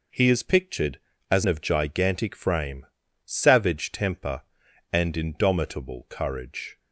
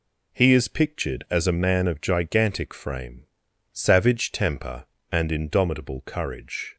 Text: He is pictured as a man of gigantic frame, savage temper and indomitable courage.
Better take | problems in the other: second | skips "a man"; at 1.4 s

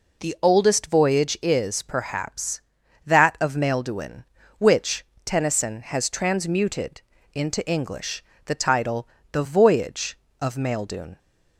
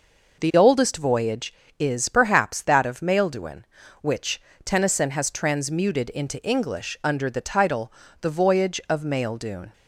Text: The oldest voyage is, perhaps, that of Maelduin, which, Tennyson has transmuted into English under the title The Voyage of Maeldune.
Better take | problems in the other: second | pauses between "transmuted" and "into"; slight; at 7.0 s; 0.32 s long // skips "under"; at 8.3 s // pauses between "title" and "The"; slight; at 9.0 s; 0.24 s long; slight in the second

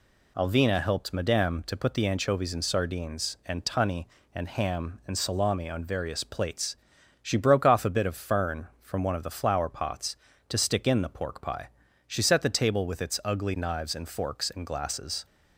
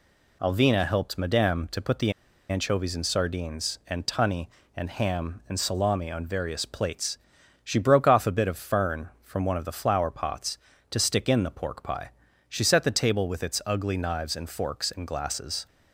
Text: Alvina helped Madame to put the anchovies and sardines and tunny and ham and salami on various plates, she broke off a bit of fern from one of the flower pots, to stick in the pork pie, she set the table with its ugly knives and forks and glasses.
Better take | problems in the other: first | pauses between "the" and "anchovies"; at 2.1 s; 0.37 s long

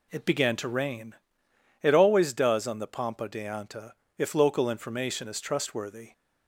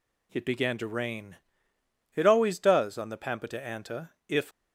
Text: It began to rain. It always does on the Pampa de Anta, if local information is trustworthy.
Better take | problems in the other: first | stops before "local information is trustworthy"; at 4.5 s

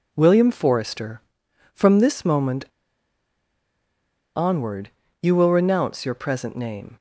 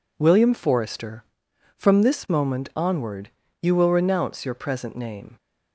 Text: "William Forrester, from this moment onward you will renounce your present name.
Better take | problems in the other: second | pauses between "moment" and "onward"; strong; at 2.6 s; 1.6 s long // pauses between "onward" and "you"; slight; at 4.8 s; 0.32 s long; slight in the second

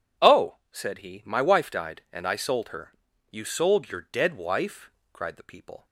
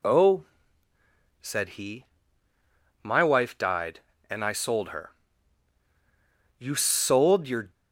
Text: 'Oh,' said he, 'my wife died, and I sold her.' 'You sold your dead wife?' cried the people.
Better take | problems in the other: first | stops before "dead wife cried the people"; at 7.7 s

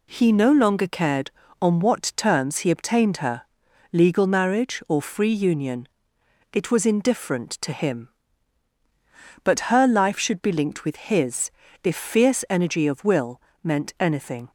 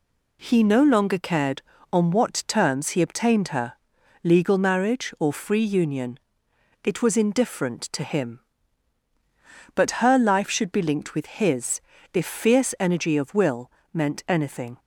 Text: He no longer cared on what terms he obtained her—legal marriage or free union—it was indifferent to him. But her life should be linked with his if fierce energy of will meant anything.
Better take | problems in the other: neither | pauses between "his" and "if"; slight; the same in both // pauses between "will" and "meant"; slight; the same in both

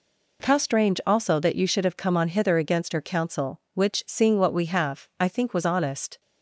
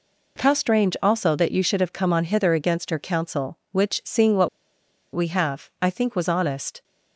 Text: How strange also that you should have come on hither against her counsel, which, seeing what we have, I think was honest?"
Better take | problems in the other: first | pauses between "what" and "we"; noticeable; at 4.4 s; 0.66 s long

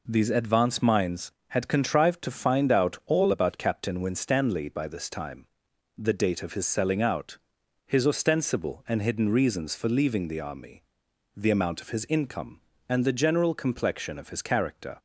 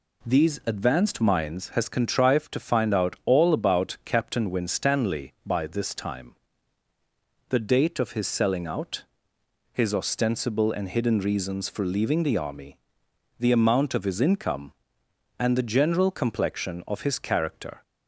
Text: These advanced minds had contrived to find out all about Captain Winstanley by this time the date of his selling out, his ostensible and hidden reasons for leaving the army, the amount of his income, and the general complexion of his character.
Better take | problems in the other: first | says "has" for "had"; at 1.6 s // pauses between "time" and "the"; at 6.3 s; 1.1 s long; noticeable in the first

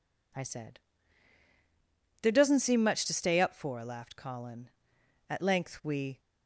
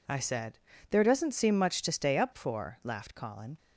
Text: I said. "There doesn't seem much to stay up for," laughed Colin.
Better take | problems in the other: second | goes on to say "At length we"; noticeable; from 5.2 s on; 0.91 s long

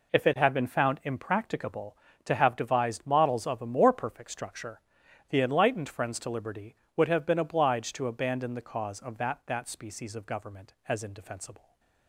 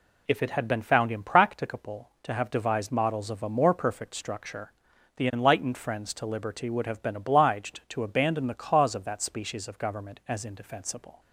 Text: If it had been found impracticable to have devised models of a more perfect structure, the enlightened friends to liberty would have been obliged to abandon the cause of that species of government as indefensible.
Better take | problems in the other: second | says "that" twice; at 9.4 s // stays silent after the last word; slight; from 11.5 s on; 0.5 s long

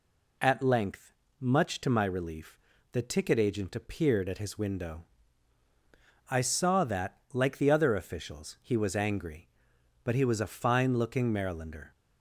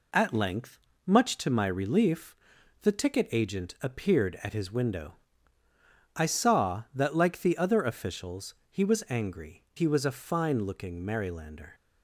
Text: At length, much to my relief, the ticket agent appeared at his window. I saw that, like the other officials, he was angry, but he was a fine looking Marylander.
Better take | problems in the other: first | skips "but"; at 9.7 s

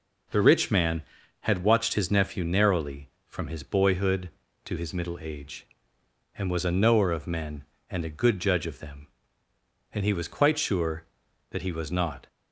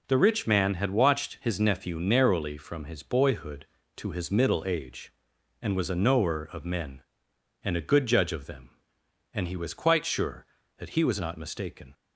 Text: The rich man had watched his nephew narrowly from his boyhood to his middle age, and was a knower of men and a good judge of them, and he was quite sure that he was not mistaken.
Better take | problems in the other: second | stops before "mistaken"; at 12.2 s

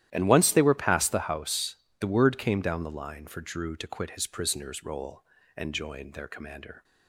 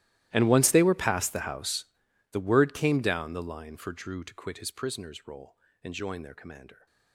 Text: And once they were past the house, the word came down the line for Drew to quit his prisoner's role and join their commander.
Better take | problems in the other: first | gets quieter; strong; throughout; 24 dB // starts louder than the rest; strong; until 1.3 s; 15 dB; strong in the first

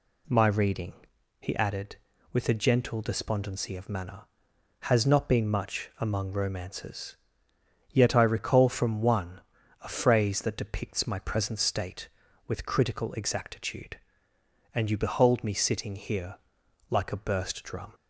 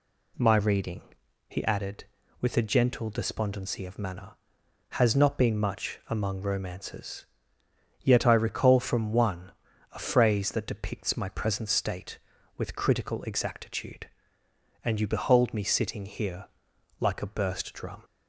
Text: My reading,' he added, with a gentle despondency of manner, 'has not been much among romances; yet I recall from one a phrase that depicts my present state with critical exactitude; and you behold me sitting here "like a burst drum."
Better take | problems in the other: neither | pauses between "one" and "a"; the same in both // pauses between "here" and "like"; noticeable; the same in both

